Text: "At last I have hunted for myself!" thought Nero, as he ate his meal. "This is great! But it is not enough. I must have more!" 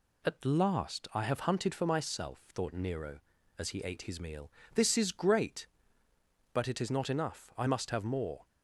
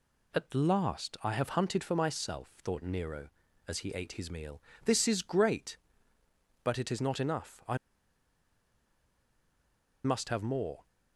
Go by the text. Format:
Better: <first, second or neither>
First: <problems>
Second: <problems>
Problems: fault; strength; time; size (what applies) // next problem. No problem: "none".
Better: first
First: none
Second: pauses between "I" and "must"; strong; at 7.7 s; 2.2 s long